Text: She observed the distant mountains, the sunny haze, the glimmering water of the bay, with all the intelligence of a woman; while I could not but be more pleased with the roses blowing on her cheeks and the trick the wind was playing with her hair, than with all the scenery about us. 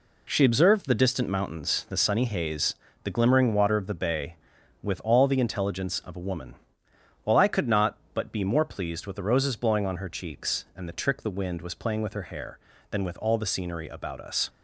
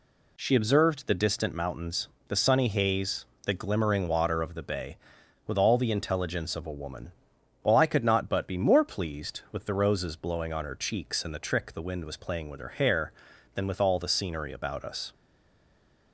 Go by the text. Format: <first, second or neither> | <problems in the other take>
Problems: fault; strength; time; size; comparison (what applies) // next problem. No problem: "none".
first | stays silent after the last word; from 15.1 s on; 1.0 s long